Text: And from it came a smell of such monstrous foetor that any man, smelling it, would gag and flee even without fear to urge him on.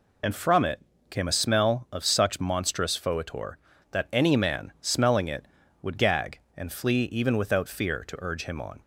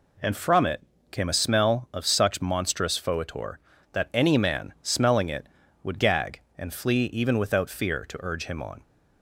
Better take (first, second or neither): second